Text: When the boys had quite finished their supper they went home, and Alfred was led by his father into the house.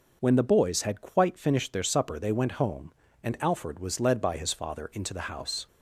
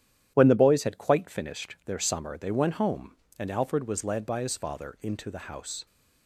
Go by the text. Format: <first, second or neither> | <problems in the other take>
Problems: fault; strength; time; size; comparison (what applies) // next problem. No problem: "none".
first | starts louder than the rest; strong; until 1.3 s; 11 dB // says "summer" for "supper"; at 1.9 s